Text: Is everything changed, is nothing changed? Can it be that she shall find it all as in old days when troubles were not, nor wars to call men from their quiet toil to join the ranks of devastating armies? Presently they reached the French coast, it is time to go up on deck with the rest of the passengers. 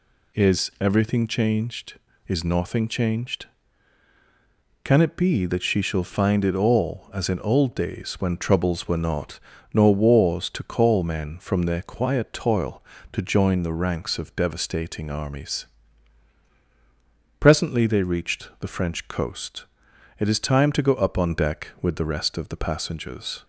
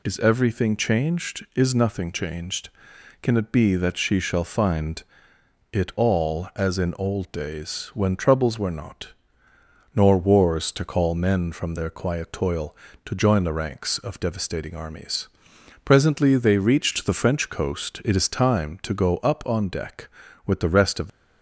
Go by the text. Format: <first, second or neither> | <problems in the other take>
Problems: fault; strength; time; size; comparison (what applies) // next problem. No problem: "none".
first | pauses between "find" and "it"; noticeable; at 5.0 s; 0.70 s long // stops before "the passengers"; at 21.0 s